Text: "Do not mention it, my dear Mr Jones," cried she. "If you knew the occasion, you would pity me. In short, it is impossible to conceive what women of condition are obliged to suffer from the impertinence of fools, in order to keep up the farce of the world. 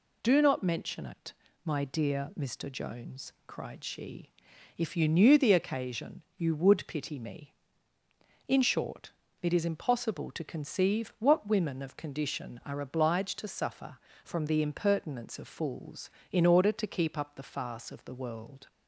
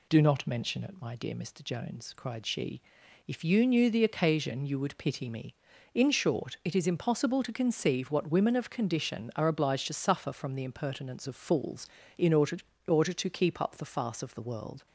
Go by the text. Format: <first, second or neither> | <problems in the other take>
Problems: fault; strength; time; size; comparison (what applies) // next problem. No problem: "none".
first | says "order" twice; at 12.8 s